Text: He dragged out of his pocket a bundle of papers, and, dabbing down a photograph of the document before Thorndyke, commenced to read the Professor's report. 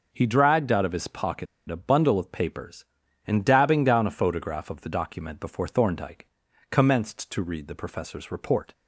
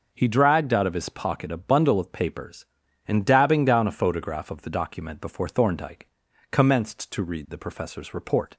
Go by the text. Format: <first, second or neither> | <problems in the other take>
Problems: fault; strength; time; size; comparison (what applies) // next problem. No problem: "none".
second | pauses between "pocket" and "a"; slight; at 1.4 s; 0.23 s long